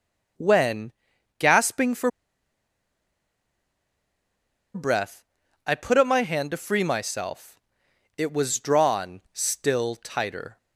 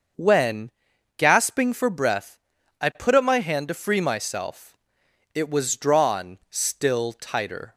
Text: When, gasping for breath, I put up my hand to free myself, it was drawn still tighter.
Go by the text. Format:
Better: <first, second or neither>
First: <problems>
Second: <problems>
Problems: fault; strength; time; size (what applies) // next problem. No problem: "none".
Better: second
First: starts louder than the rest; until 1.8 s; 6 dB // pauses between "for" and "breath"; strong; at 2.1 s; 2.6 s long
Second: starts louder than the rest; until 1.6 s; 6.5 dB